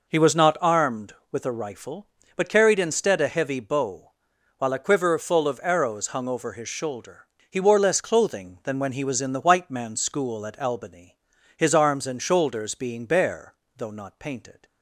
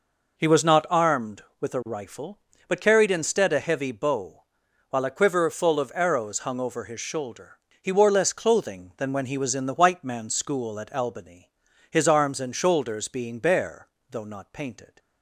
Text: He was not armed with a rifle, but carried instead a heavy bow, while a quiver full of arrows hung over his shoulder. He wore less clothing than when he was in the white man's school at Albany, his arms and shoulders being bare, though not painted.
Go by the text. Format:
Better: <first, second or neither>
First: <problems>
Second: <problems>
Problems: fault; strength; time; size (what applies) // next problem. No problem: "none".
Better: neither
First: none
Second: none